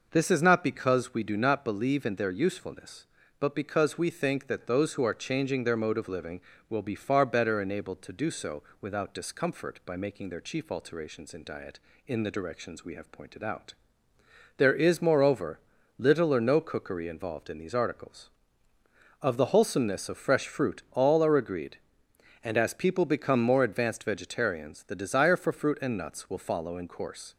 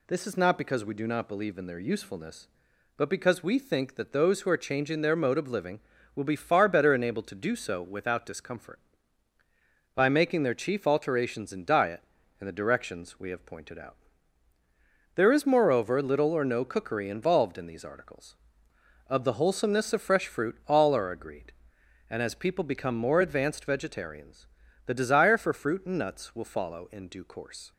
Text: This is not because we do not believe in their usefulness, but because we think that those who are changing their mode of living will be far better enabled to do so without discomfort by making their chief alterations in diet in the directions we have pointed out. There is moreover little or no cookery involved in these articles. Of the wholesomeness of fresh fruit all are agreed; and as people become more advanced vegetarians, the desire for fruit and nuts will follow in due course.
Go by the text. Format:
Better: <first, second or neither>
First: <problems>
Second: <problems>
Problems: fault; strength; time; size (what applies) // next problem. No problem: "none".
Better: second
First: pauses between "so" and "without"; slight; at 8.6 s; 0.18 s long // pauses between "moreover" and "little"; at 15.5 s; 0.40 s long // skips "due"; at 26.8 s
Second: none